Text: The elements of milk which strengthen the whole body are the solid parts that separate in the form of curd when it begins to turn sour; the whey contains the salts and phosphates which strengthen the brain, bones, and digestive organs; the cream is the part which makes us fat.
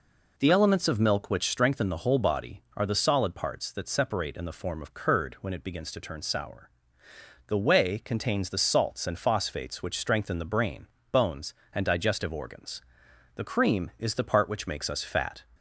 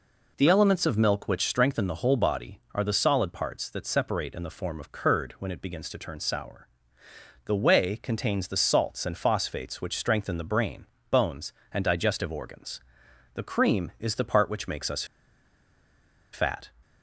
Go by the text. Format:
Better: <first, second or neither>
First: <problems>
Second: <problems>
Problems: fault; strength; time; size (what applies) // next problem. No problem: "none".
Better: first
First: none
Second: pauses between "us" and "fat"; strong; at 15.0 s; 1.2 s long